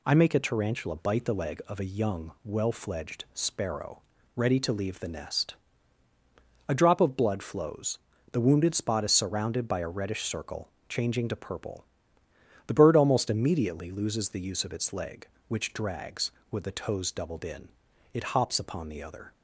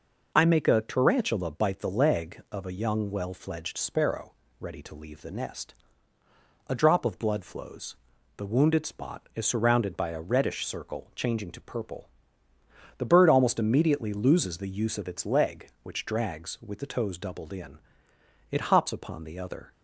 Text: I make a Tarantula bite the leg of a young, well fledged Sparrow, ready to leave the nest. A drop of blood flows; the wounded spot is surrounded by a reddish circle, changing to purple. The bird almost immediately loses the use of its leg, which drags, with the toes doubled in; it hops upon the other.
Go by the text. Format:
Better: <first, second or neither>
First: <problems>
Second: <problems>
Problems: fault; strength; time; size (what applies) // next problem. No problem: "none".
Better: neither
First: none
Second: none